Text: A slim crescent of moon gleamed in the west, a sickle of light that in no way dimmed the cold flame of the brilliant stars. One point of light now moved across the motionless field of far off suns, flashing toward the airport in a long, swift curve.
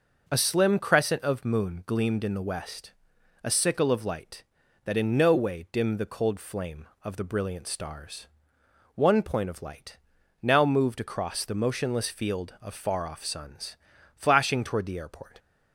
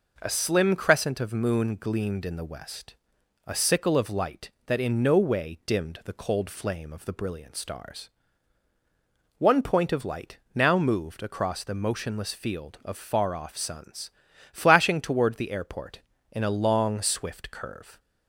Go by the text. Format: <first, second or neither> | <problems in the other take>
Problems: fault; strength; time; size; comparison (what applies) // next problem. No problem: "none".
second | pauses between "light" and "now"; at 9.9 s; 0.44 s long; slight in the second // stops before "in a long swift curve"; at 15.3 s